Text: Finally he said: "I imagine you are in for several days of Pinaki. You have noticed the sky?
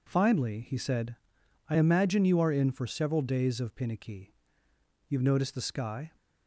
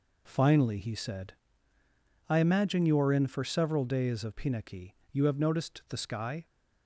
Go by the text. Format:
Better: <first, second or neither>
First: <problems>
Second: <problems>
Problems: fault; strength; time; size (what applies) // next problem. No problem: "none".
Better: neither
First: none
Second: none